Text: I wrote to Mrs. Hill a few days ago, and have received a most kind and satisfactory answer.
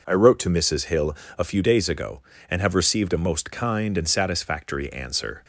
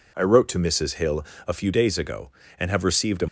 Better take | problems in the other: first | pauses between "Hill" and "a"; slight; at 1.2 s; 0.24 s long; slight in the first // stops before "most kind and satisfactory answer"; at 3.2 s

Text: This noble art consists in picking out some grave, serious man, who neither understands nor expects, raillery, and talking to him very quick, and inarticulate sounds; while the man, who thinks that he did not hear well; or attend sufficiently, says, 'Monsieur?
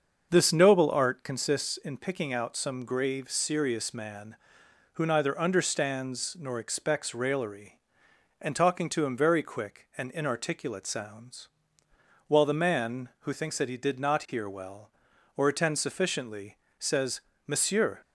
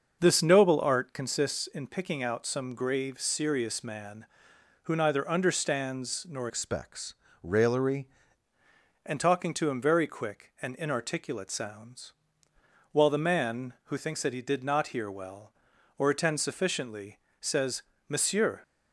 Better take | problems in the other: first | starts louder than the rest; until 1.2 s; 6 dB; also in the first // changes voice from "expects" to "raillery"; from 6.4 to 8.0 s; 1.6 s long

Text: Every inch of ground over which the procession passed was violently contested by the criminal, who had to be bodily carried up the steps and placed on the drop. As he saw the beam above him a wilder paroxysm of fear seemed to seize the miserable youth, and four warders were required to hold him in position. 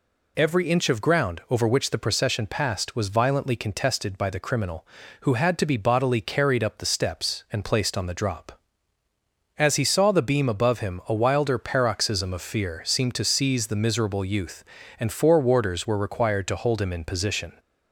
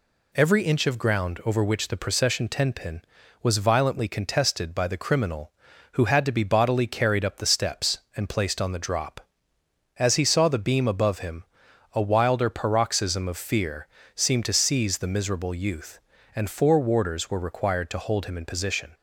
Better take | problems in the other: first | says "tenpin" for "passed"; at 2.4 s // pauses between "him" and "a"; noticeable; at 11.4 s; 0.50 s long // pauses between "fear" and "seemed"; slight; at 13.8 s; 0.28 s long

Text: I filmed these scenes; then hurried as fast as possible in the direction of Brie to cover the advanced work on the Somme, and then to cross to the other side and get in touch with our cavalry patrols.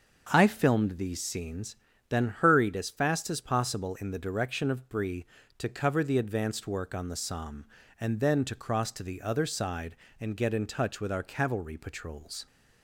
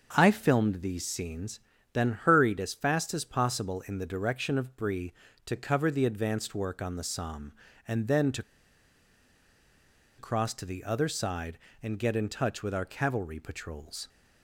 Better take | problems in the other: first | starts louder than the rest; until 1.1 s; 6.5 dB; also in the first // pauses between "to" and "cross"; strong; at 8.4 s; 1.7 s long

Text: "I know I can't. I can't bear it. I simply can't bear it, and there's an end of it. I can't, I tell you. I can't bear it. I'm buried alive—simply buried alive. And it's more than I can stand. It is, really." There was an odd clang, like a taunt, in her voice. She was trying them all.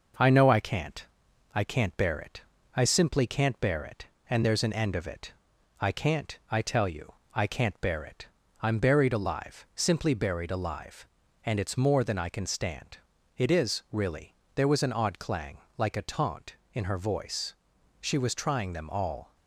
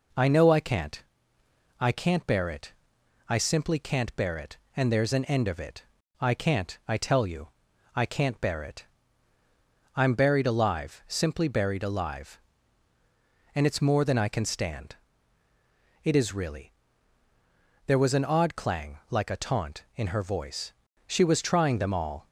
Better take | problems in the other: second | gets quieter; slight; throughout; 2.5 dB

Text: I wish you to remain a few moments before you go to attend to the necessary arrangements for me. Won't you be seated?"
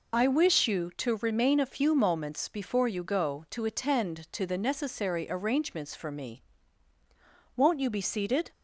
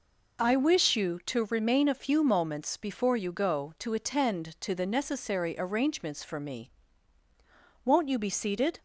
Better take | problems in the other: second | loses the start of "I"; at 0.1 s; 30 ms

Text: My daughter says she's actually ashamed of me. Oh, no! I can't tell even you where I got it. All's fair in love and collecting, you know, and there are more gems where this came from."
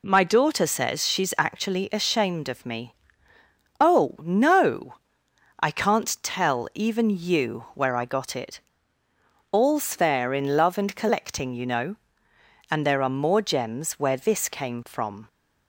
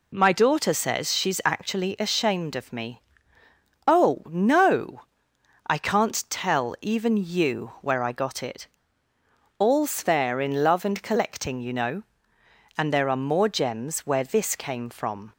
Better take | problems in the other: neither | none

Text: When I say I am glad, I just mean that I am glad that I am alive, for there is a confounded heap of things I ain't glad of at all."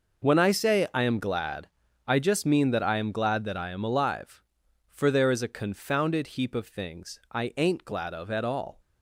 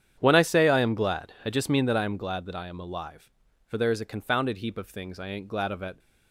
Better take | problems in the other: first | starts louder than the rest; strong; until 1.2 s; 9 dB // stops before "all"; at 5.9 s

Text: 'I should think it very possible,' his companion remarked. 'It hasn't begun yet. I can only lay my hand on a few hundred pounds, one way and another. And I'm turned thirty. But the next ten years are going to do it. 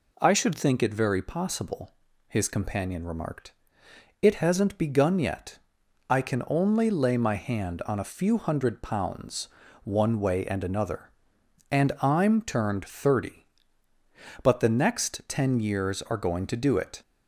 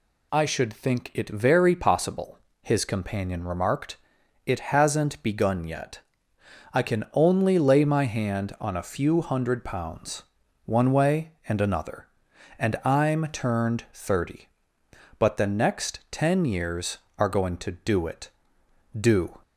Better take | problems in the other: first | goes on to say "Do"; slight; from 18.9 s on; 0.42 s long

